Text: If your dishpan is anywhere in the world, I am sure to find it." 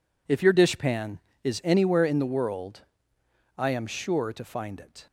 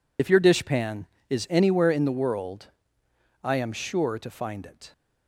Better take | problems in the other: first | loses the start of "If"; at 0.1 s; 55 ms

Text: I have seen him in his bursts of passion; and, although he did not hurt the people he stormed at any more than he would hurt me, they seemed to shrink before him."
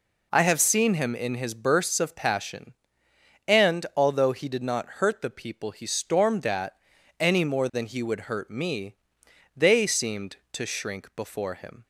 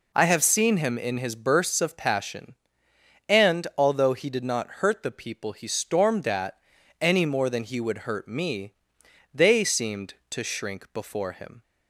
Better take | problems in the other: neither | pauses between "at" and "any"; noticeable; the same in both

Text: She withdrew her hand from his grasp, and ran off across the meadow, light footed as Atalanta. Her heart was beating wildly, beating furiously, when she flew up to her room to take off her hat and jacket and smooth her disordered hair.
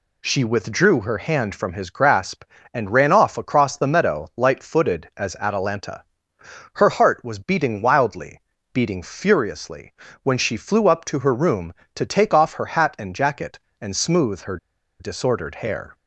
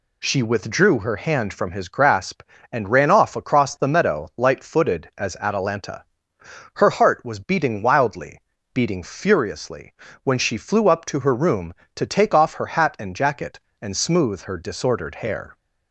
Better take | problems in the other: second | pauses between "her" and "disordered"; at 14.5 s; 0.43 s long

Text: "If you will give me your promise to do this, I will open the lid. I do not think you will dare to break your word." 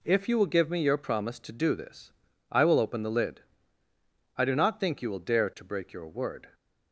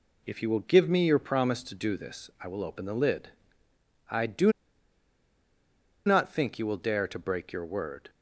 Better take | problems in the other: first | pauses between "do" and "not"; strong; at 4.5 s; 1.5 s long

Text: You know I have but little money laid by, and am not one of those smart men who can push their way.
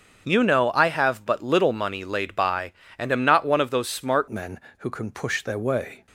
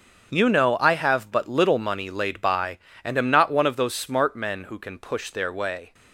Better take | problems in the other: second | starts louder than the rest; until 1.2 s; 6.5 dB; also in the second // changes voice at "men"; from 4.3 s on; 1.7 s long

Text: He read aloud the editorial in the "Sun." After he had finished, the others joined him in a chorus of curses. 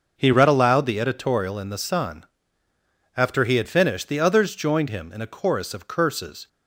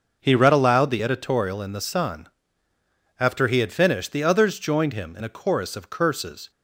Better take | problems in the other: neither | starts louder than the rest; noticeable; the same in both

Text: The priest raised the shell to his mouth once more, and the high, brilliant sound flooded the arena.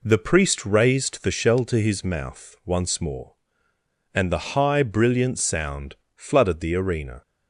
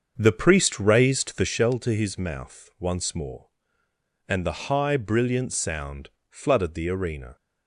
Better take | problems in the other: first | starts louder than the rest; until 1.6 s; 6.5 dB // pauses between "sound" and "flooded"; slight; at 6.0 s; 0.22 s long; slight in the first

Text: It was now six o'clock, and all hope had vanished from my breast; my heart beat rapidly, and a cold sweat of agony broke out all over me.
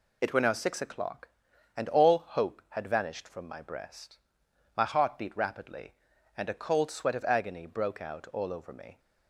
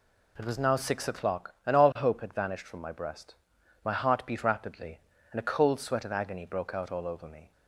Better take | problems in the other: second | says "were" for "was"; at 0.3 s

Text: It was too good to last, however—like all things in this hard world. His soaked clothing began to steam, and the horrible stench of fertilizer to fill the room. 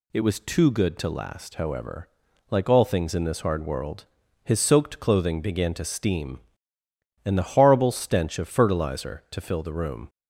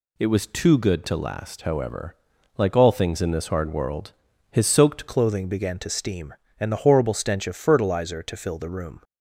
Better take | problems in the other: first | changes voice at "clothing"; from 5.0 s on; 4.0 s long

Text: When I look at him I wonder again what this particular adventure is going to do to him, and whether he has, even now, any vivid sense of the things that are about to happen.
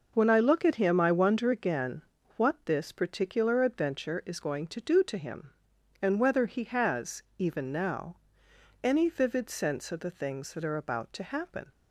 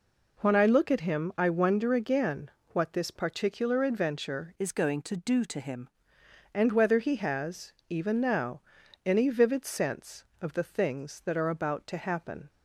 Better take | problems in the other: first | pauses between "again" and "what"; slight; at 2.4 s; 0.24 s long; slight in the first // changes voice from "is" to "him"; from 4.5 to 5.8 s; 1.3 s long

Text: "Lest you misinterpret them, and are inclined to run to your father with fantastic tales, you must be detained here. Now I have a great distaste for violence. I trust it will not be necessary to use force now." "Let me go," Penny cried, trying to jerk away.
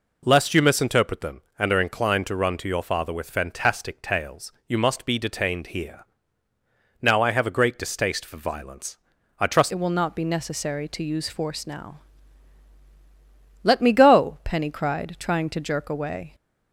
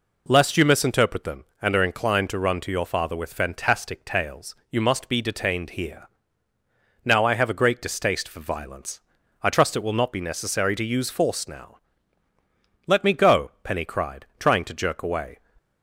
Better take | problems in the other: second | changes voice at "it"; from 9.7 s on; 6.6 s long

